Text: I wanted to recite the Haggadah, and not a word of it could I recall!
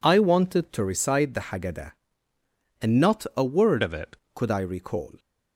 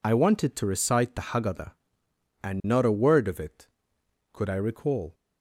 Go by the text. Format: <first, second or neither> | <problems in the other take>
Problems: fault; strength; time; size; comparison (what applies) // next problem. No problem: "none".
second | changes voice from "of" to "it"; from 3.8 to 4.1 s; 0.3 s long